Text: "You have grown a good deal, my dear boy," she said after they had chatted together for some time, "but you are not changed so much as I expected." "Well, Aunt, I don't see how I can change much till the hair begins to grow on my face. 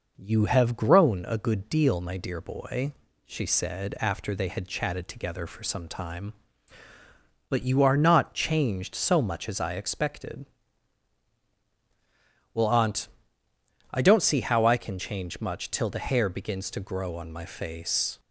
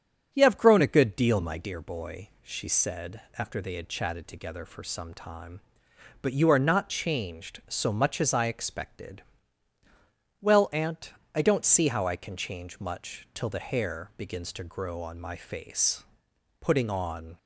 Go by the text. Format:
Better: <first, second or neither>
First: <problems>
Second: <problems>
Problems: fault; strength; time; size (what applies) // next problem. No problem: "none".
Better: first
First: none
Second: starts louder than the rest; strong; until 1.3 s; 8.5 dB // pauses between "said" and "after"; slight; at 3.2 s; 0.18 s long // goes on to say "Putting on"; noticeable; from 16.5 s on; 0.78 s long